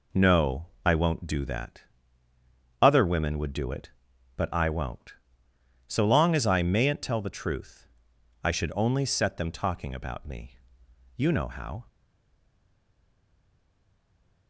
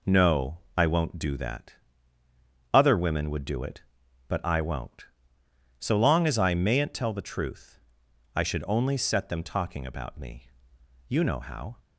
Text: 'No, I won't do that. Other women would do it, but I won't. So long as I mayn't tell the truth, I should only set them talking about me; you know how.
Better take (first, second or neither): second